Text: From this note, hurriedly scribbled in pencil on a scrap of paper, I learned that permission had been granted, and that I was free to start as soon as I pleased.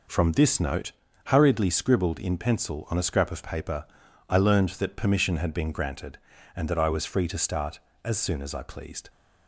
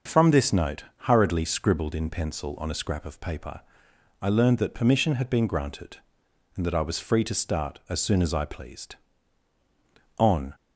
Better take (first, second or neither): first